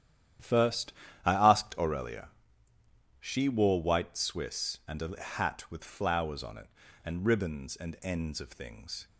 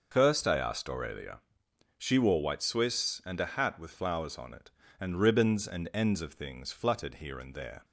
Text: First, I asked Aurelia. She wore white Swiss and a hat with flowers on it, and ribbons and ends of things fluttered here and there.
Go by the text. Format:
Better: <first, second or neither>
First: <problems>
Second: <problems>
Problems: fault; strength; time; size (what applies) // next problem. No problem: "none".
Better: second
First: starts louder than the rest; strong; until 1.7 s; 10.5 dB // stops before "fluttered here and there"; at 9.0 s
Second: none